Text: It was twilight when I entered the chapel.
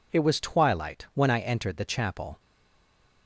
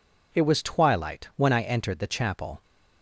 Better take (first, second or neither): second